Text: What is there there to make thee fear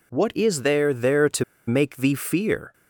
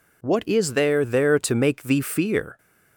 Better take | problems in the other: second | pauses between "to" and "make"; slight; at 1.4 s; 0.24 s long

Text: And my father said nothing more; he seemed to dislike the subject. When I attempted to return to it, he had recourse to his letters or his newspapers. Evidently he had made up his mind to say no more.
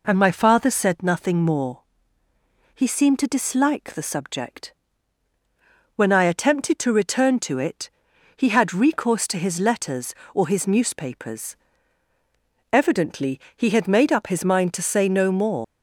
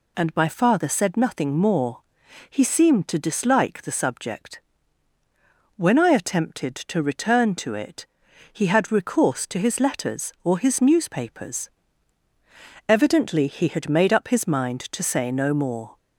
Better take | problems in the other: second | pauses between "Evidently" and "he"; slight; at 13.3 s; 0.16 s long // leaves "more" unfinished; at 15.6 s; 90 ms

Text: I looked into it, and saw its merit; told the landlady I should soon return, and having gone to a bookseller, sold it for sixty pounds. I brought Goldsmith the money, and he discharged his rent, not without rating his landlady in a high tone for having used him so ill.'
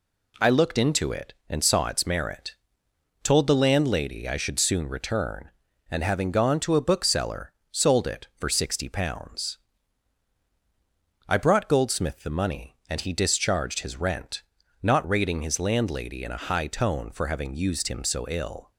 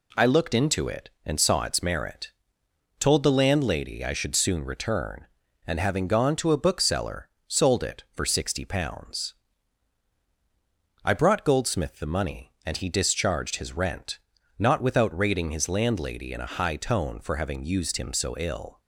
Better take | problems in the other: second | skips "without"; at 15.0 s

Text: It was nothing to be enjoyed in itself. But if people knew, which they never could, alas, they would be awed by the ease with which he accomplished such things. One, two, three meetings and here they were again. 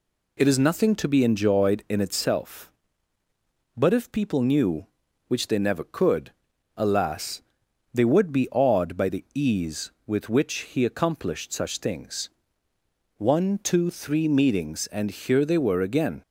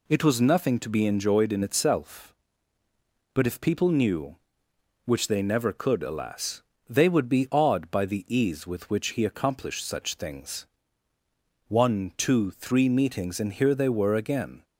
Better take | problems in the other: second | says "is" for "was"; at 0.4 s

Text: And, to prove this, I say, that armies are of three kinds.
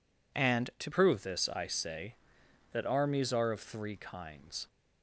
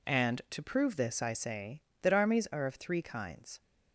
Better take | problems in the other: second | changes voice at "prove"; from 0.9 s on; 3.7 s long

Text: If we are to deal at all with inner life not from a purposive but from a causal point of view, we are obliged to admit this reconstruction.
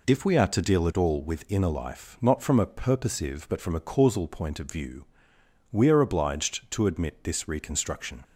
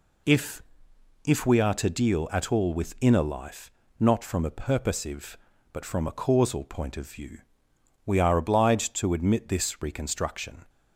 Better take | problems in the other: first | says "If" twice; at 1.2 s // pauses between "life" and "not"; slight; at 3.7 s; 0.26 s long

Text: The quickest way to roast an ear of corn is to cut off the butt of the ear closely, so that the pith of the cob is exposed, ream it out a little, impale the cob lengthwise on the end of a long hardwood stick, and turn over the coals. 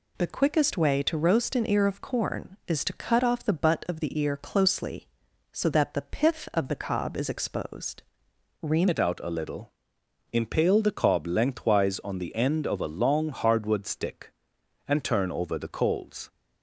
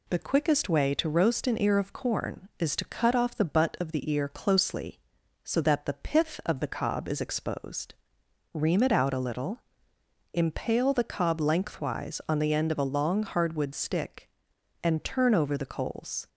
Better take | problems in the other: second | changes voice at "it"; from 8.8 s on; 7.4 s long

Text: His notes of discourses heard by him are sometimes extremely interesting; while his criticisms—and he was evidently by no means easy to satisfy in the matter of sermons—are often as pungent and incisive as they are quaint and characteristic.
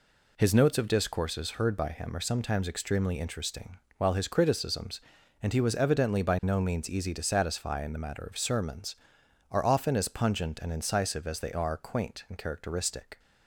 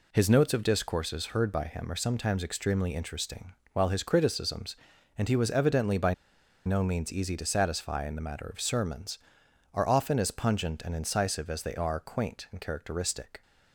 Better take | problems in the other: first | pauses between "by" and "no"; noticeable; at 6.1 s; 0.51 s long

